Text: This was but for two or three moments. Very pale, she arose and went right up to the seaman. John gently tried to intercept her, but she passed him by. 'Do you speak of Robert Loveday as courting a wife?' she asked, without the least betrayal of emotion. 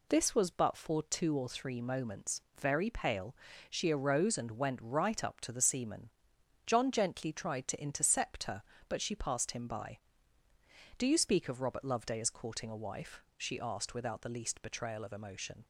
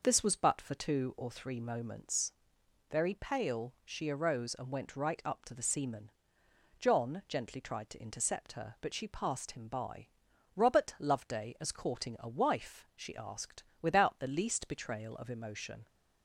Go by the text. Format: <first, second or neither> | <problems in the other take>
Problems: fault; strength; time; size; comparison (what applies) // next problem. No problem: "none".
first | skips "Do you speak of"; at 10.3 s